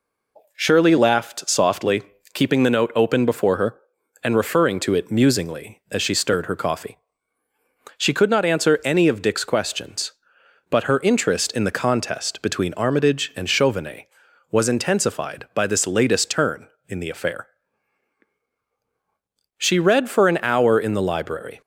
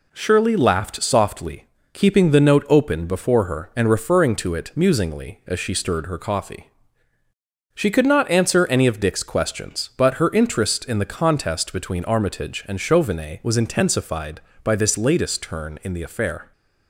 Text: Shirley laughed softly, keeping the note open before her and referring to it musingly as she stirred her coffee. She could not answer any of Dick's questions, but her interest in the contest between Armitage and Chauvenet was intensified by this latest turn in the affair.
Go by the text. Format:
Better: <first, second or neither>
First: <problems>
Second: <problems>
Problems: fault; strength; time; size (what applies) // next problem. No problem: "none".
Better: second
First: goes on to say "She read for an hour in the library"; strong; from 19.5 s on; 2.0 s long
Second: none